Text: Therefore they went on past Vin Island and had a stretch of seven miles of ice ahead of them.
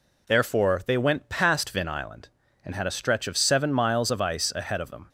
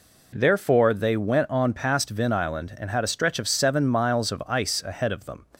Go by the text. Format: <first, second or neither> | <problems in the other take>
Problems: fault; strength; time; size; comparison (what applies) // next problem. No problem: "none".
second | skips "on"; at 1.2 s